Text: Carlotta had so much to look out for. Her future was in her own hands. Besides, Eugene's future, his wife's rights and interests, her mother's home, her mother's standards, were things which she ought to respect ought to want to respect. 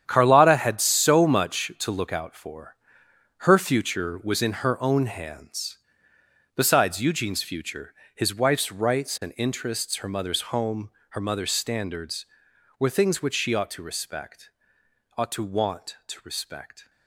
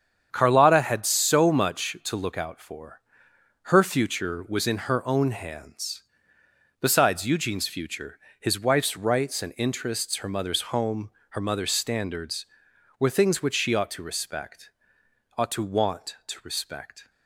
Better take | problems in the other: second | gets quieter; strong; throughout; 11.5 dB // starts louder than the rest; strong; until 1.0 s; 9 dB; strong in the second // pauses between "respect" and "ought"; noticeable; at 14.4 s; 0.68 s long; noticeable in the second

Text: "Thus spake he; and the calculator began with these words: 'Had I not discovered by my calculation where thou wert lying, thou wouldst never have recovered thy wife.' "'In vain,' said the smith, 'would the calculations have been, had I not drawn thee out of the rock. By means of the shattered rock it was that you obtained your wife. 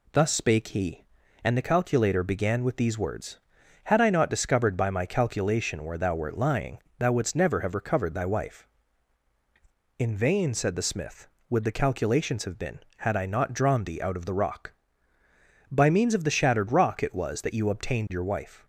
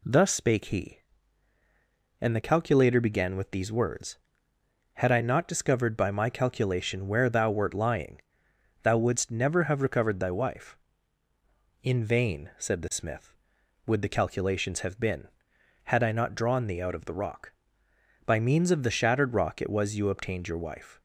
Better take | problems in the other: first | skips "that"; at 19.9 s

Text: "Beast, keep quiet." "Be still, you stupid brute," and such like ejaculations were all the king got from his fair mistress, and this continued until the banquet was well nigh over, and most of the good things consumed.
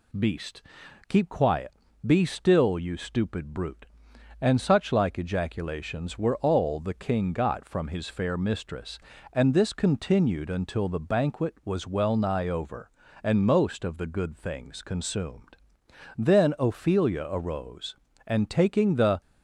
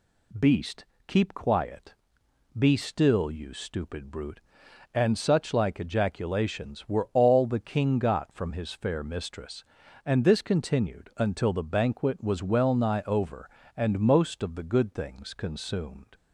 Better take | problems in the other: second | goes on to say "Then Ophelia arose and taking the"; strong; from 16.1 s on; 3.0 s long

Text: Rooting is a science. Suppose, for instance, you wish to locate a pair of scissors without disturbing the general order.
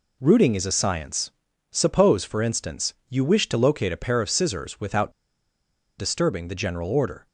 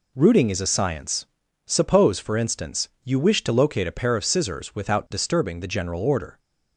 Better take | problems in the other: second | pauses between "without" and "disturbing"; noticeable; at 5.1 s; 0.86 s long

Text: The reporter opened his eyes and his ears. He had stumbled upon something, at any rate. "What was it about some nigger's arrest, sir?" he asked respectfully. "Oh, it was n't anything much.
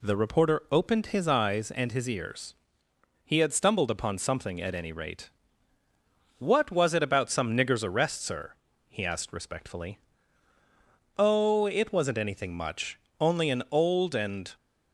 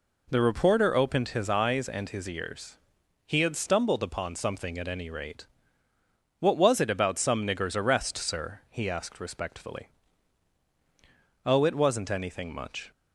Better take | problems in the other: second | goes on to say "Only an old and"; from 13.1 s on; 1.3 s long

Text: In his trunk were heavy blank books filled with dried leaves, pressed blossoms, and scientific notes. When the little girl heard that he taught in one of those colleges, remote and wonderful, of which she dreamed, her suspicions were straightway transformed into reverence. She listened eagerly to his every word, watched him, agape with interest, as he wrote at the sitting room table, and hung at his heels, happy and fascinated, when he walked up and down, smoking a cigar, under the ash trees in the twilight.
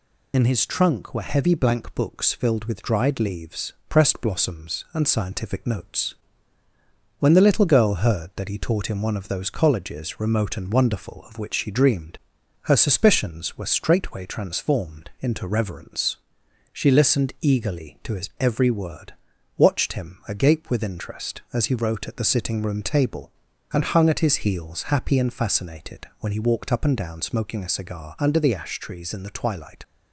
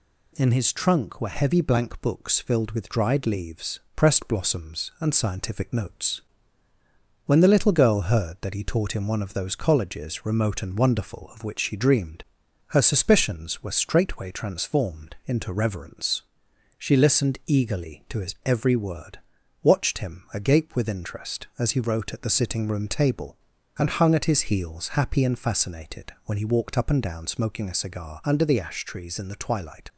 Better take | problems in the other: second | loses the start of "In"; at 0.3 s; 60 ms

